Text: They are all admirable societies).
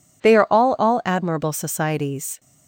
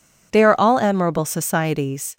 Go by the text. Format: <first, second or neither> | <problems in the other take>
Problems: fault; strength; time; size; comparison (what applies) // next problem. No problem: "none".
second | says "all" twice; at 0.7 s